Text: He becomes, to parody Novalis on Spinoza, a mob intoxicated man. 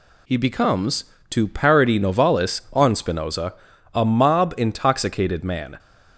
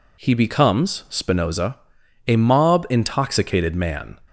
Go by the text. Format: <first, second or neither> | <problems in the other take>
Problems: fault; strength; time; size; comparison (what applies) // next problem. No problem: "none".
first | skips "to parody Novalis on"; at 1.0 s